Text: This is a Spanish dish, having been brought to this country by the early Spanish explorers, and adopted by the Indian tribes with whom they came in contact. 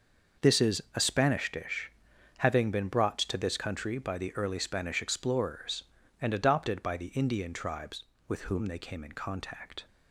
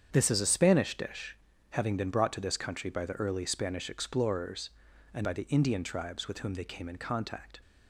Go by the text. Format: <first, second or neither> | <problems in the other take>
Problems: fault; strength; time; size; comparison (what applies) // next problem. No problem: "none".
first | starts louder than the rest; strong; until 1.1 s; 8 dB // skips "adopted"; at 5.2 s